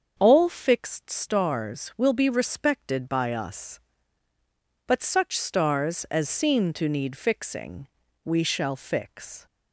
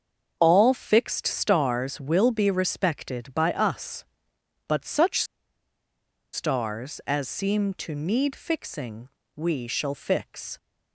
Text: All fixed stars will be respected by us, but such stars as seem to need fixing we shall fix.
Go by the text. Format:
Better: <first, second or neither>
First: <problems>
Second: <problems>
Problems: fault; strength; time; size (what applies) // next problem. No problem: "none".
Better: first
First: starts louder than the rest; until 1.1 s; 7 dB // pauses between "fixing" and "we"; slight; at 7.8 s; 0.36 s long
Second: starts louder than the rest; until 1.4 s; 7 dB // pauses between "such" and "stars"; at 5.2 s; 1.0 s long // pauses between "fixing" and "we"; slight; at 9.0 s; 0.26 s long